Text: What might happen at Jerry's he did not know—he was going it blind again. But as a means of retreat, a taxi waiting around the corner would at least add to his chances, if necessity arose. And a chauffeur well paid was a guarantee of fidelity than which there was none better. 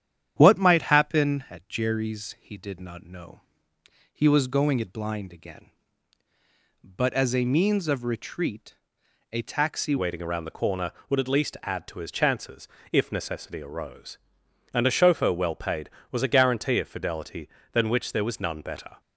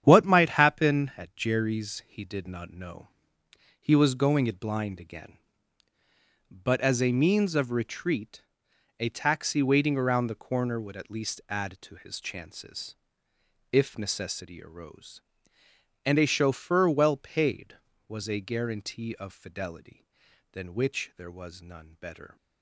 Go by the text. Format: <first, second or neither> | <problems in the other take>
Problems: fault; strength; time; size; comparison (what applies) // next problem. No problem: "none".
second | starts louder than the rest; strong; until 1.3 s; 9.5 dB; strong in the second // changes voice at "waiting"; from 9.9 s on; 9.0 s long